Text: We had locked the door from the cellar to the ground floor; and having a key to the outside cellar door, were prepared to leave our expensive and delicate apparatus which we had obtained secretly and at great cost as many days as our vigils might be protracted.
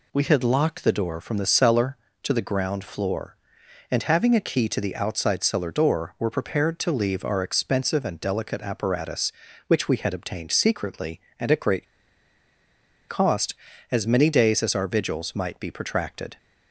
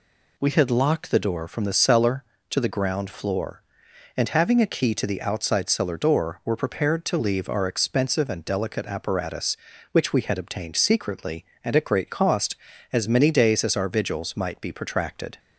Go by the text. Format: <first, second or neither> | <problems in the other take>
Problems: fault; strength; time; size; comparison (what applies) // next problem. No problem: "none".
second | pauses between "great" and "cost"; at 11.8 s; 1.2 s long